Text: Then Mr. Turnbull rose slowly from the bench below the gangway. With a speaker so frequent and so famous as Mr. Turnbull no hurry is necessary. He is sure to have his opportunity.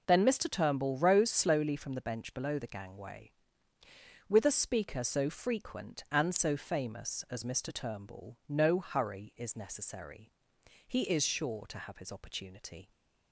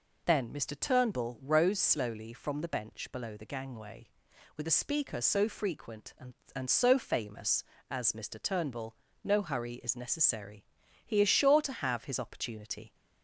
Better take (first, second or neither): first